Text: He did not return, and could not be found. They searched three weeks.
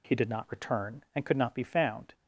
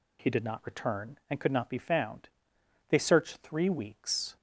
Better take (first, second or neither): second